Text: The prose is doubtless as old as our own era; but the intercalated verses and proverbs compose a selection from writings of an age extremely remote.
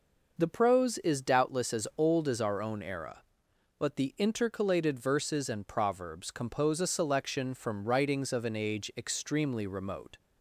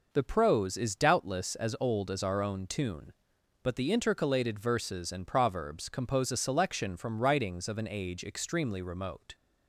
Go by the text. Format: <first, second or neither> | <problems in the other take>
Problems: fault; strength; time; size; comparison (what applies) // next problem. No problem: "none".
first | says "tune" for "era"; at 2.6 s